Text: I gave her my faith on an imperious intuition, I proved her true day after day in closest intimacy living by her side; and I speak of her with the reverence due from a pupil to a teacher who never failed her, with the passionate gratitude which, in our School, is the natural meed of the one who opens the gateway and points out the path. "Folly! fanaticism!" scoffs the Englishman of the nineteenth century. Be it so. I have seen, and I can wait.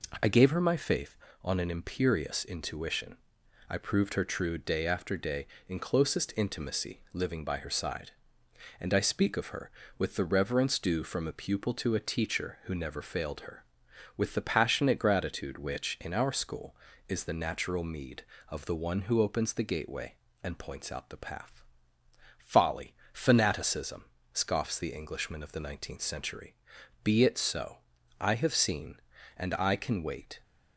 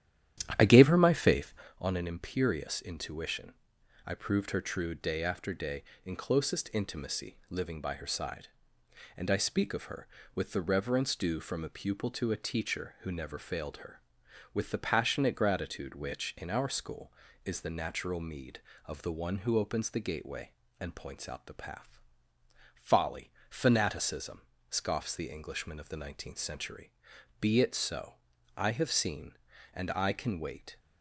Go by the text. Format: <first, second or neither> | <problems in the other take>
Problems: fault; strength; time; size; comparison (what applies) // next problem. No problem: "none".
first | starts louder than the rest; strong; until 1.9 s; 11 dB